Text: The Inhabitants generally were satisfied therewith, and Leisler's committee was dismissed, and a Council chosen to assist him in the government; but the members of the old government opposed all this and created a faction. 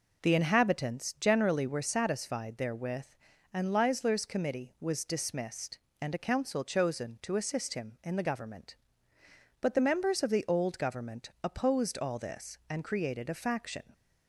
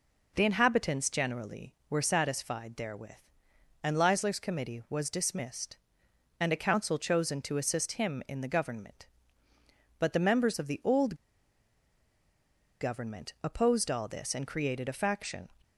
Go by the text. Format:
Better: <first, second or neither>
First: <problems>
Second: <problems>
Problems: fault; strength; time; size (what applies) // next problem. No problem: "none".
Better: first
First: none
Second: pauses between "old" and "government"; strong; at 11.1 s; 1.6 s long